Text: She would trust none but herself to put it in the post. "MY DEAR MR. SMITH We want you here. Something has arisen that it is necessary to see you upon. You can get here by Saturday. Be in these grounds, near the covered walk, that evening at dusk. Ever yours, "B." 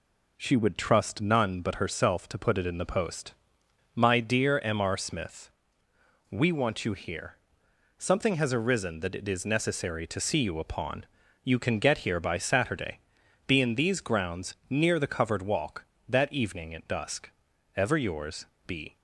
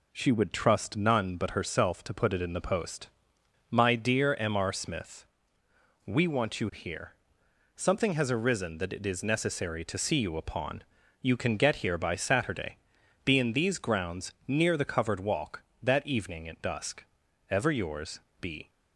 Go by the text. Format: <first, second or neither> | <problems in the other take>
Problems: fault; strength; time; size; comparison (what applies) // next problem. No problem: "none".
neither | pauses between "SMITH" and "We"; noticeable; the same in both